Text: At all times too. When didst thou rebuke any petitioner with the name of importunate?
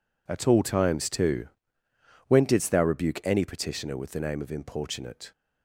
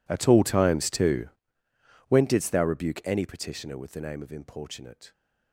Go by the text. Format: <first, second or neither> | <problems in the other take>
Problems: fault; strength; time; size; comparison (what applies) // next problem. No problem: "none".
first | gets quieter; strong; throughout; 23 dB